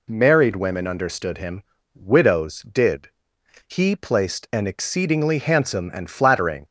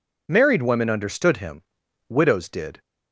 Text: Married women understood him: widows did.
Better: second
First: goes on to say "He placed an exceedingly handsome and flattering"; strong; from 3.6 s on; 2.9 s long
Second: none

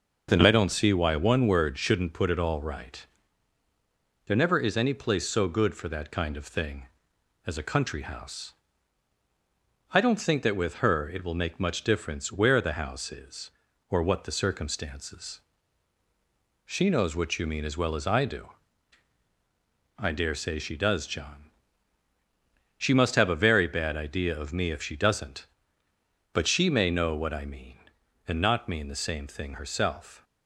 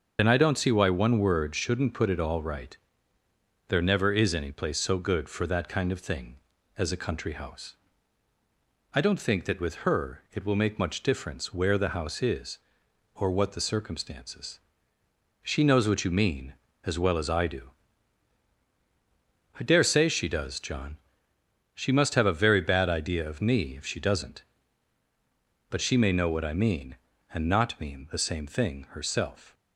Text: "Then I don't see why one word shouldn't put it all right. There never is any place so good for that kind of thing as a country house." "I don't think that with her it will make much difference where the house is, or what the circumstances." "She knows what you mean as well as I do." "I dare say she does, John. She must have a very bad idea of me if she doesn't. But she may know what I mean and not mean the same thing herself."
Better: first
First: none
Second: loses the start of "Then"; at 0.1 s; 55 ms // starts louder than the rest; until 1.2 s; 6.5 dB

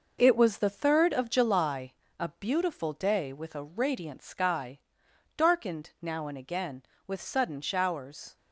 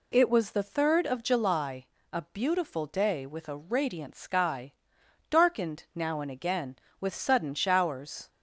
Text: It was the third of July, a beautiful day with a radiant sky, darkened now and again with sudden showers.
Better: second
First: gets quieter; noticeable; throughout; 6 dB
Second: none

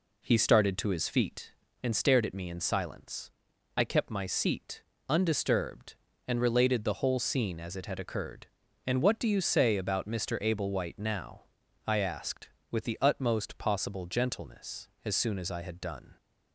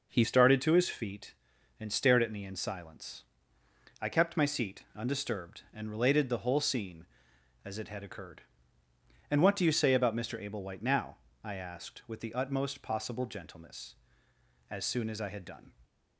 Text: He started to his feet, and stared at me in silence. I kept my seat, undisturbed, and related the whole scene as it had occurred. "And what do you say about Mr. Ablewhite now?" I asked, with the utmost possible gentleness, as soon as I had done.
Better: first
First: none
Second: changes voice at "started"; from 0.2 s on; 15.5 s long

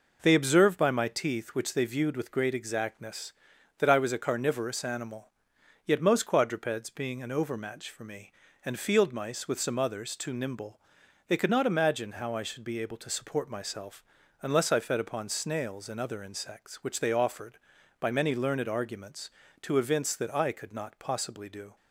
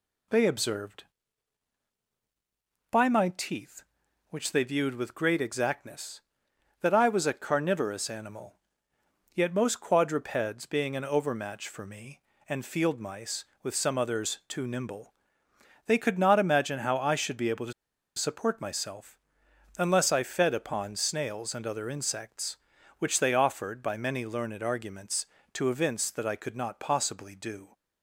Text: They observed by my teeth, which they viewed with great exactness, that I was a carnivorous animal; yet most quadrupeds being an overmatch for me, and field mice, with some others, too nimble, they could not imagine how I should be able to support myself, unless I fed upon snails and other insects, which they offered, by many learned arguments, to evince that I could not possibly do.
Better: first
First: none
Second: pauses between "to" and "support"; at 17.7 s; 0.44 s long

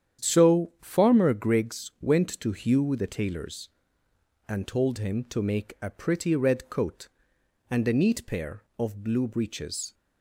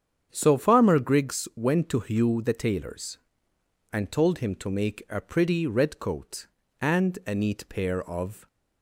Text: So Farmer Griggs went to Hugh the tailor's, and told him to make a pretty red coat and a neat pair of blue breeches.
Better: first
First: starts louder than the rest; strong; until 1.3 s; 9 dB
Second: starts louder than the rest; strong; until 1.3 s; 8 dB // stops before "blue breeches"; at 8.4 s

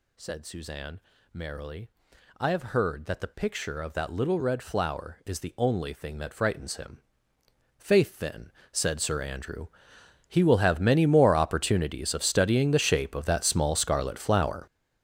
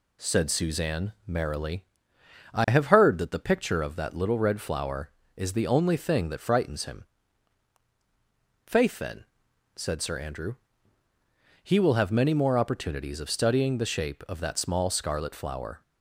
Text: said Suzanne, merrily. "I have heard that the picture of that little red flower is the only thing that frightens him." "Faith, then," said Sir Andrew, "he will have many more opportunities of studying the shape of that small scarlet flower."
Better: second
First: gets louder; strong; throughout; 13 dB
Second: none

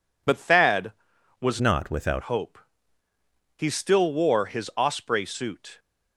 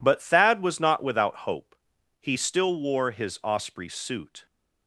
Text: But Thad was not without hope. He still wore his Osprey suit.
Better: second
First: changes voice from "not" to "without"; from 1.6 to 2.2 s; 0.6 s long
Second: none

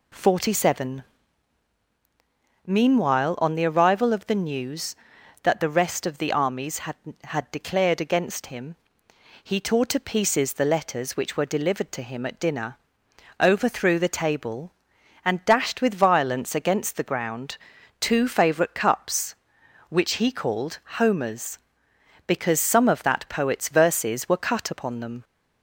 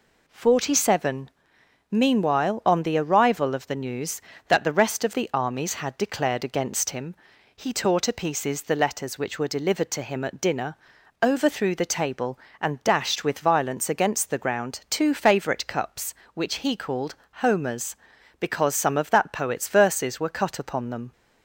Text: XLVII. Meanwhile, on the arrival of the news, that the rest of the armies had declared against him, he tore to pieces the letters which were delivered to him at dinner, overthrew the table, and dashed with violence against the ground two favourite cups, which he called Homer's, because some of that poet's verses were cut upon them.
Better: second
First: says "had" twice; at 7.2 s // pauses between "ground" and "two"; at 17.5 s; 0.42 s long // pauses between "called" and "Homer's"; slight; at 20.7 s; 0.22 s long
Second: pauses between "called" and "Homer's"; slight; at 17.1 s; 0.20 s long

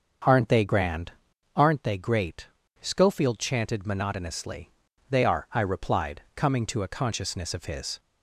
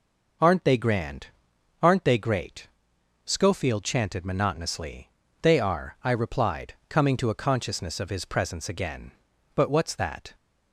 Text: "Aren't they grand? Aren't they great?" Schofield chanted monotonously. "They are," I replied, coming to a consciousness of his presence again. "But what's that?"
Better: second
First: starts louder than the rest; until 1.7 s; 7 dB // stops before "presence again But what's that"; at 7.9 s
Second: none

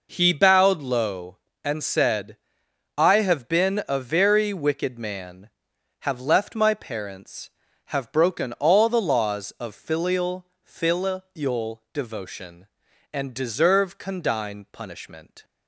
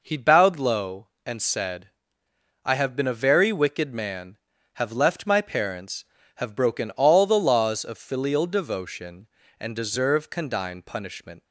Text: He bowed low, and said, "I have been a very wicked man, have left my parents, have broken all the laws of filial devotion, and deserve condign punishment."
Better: second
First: says "filial" twice; at 10.6 s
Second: none

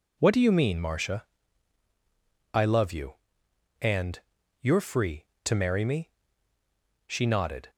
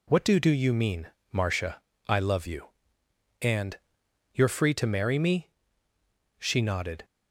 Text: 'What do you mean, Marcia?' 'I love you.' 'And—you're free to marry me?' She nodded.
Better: first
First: none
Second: says "do" twice; at 0.3 s

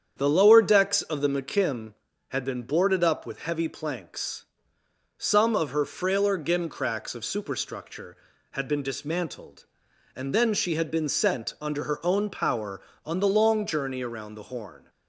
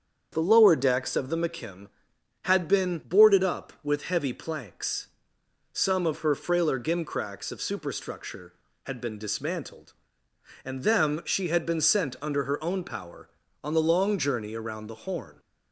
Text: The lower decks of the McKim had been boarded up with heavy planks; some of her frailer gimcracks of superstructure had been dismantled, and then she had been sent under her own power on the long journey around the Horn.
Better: first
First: starts louder than the rest; strong; until 1.1 s; 8 dB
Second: starts louder than the rest; strong; until 1.3 s; 7.5 dB // says "them" for "then"; at 10.8 s

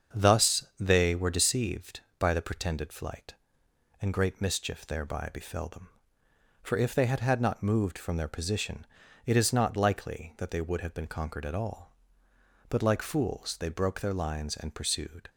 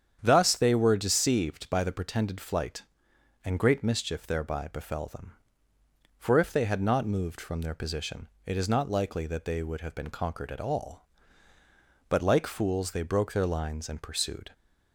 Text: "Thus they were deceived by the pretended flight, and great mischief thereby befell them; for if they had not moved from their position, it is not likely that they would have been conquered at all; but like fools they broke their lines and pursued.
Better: second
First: starts louder than the rest; until 1.2 s; 7 dB // says "had" twice; at 7.2 s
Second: starts louder than the rest; strong; until 1.2 s; 8.5 dB

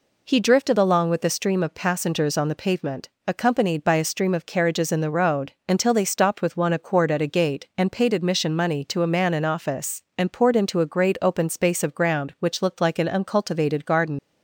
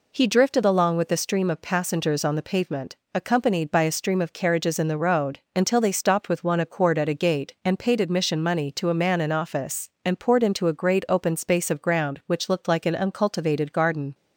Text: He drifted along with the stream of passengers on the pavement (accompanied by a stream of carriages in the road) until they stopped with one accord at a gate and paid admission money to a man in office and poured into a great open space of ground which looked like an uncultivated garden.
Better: second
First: leaves "garden" unfinished; at 14.1 s; 85 ms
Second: none

